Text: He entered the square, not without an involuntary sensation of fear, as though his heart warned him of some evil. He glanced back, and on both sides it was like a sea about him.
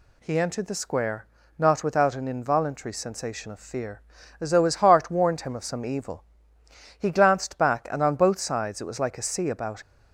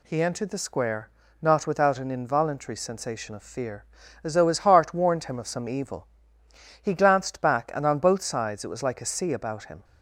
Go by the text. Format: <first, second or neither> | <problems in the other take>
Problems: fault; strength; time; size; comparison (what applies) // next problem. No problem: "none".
second | stops before "him"; at 9.8 s